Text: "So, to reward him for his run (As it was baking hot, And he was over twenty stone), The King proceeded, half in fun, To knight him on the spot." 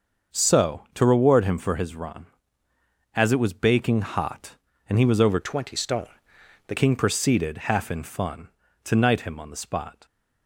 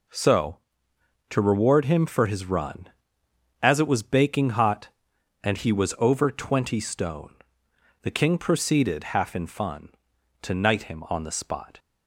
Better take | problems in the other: second | starts louder than the rest; until 1.4 s; 6.5 dB // changes voice from "twenty" to "The"; from 5.4 to 6.7 s; 1.3 s long

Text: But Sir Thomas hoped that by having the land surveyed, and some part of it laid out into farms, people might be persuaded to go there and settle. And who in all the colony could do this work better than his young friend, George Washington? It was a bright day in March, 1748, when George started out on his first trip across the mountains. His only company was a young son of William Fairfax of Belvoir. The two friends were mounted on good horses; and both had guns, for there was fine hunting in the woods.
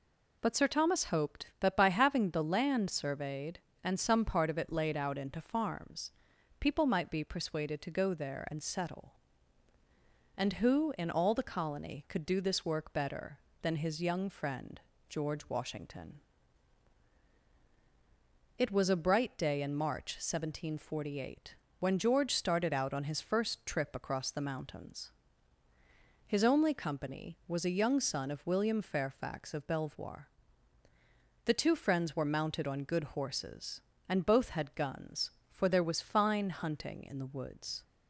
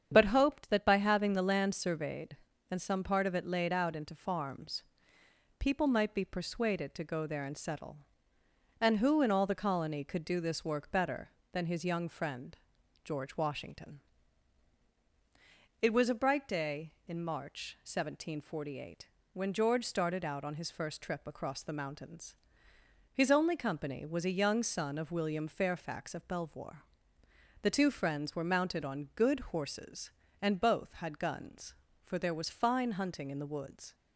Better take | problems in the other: first | starts louder than the rest; strong; until 1.1 s; 8 dB // skips "Sir Thomas"; at 0.2 s

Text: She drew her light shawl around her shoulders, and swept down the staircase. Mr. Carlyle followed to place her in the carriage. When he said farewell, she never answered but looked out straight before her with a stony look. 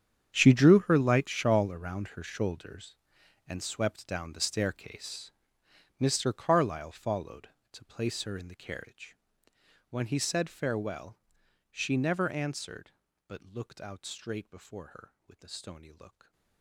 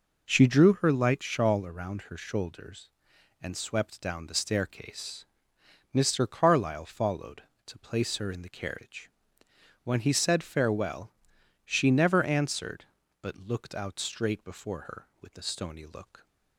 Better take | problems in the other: second | gets quieter; strong; throughout; 18 dB // stays silent after the last word; slight; from 16.0 s on; 0.6 s long

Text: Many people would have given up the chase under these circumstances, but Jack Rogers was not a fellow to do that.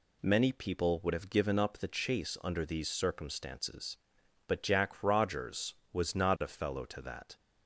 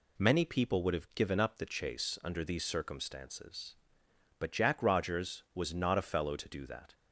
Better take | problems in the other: second | skips "do"; at 7.0 s

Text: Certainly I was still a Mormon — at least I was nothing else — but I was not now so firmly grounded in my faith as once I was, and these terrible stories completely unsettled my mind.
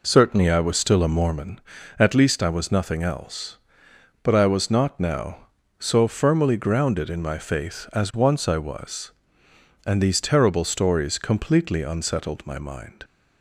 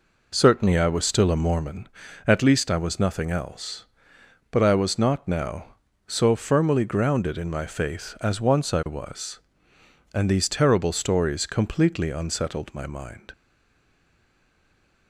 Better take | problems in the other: first | stays silent after the last word; noticeable; from 13.3 s on; 1.7 s long

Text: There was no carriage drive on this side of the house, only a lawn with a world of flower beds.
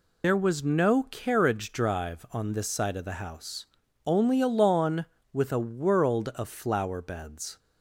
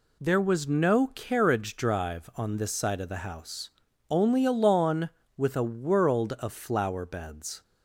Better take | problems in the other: second | loses the start of "There"; at 0.2 s; 80 ms

